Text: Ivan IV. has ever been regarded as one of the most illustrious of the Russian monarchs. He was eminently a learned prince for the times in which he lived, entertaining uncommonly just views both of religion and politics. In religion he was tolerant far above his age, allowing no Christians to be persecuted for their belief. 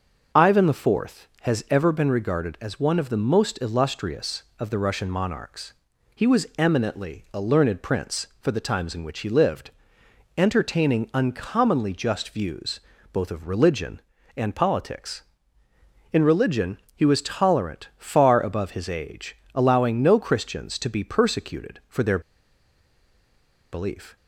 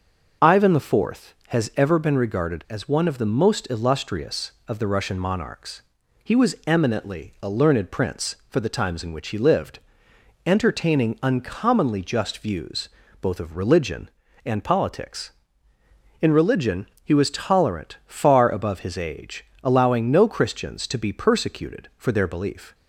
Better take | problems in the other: second | pauses between "views" and "both"; slight; at 12.7 s; 0.32 s long; slight in the second // pauses between "religion" and "he"; slight; at 16.7 s; 0.18 s long; slight in the second // pauses between "their" and "belief"; strong; at 22.1 s; 1.5 s long

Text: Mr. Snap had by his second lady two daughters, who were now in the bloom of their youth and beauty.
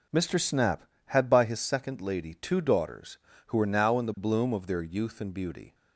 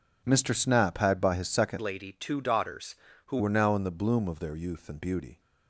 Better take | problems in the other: first | changes voice from "lady" to "who"; from 1.7 to 3.3 s; 1.6 s long

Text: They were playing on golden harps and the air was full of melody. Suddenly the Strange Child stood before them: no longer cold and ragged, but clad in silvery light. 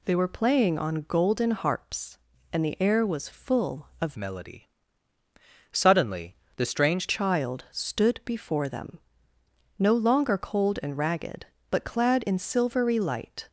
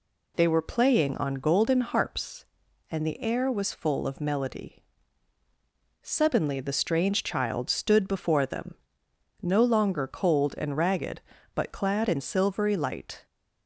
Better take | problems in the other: second | changes voice from "melody" to "Strange"; from 4.1 to 7.0 s; 2.9 s long // pauses between "Suddenly" and "the"; slight; at 6.3 s; 0.22 s long

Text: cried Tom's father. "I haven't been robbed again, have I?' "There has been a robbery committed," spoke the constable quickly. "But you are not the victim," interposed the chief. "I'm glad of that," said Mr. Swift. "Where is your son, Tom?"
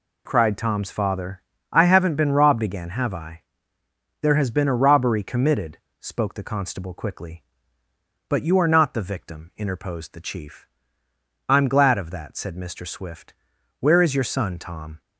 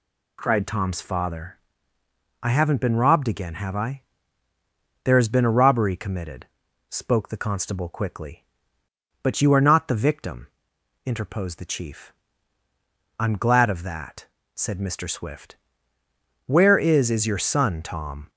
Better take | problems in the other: first | says "is" twice; at 17.0 s

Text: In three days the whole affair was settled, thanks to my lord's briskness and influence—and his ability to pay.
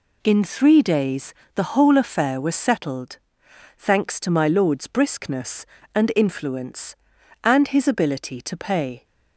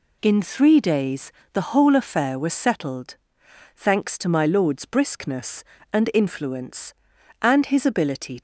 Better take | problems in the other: first | pauses between "days" and "the"; slight; at 1.3 s; 0.22 s long; slight in the first // stops before "to pay"; at 8.3 s

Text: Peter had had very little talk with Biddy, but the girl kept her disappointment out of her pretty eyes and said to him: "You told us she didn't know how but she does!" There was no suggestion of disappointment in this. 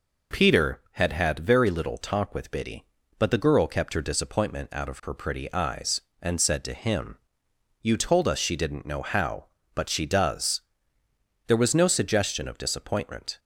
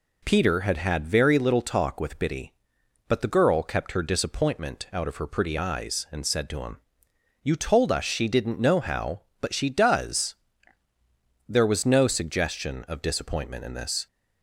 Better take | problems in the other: second | stops before "in this"; at 13.3 s

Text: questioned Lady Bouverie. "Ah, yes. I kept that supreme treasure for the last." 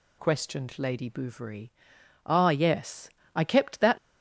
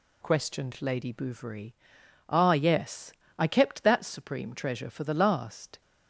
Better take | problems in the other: second | stops before "supreme treasure for the last"; at 3.9 s

